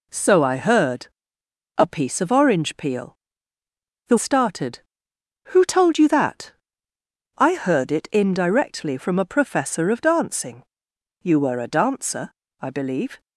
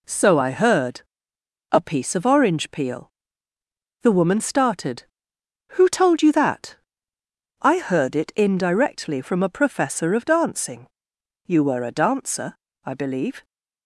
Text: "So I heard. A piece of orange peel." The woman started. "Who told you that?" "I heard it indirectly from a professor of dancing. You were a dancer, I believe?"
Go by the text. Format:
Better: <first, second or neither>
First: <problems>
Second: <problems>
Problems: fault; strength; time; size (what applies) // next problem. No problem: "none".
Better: second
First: skips "woman"; at 4.1 s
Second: none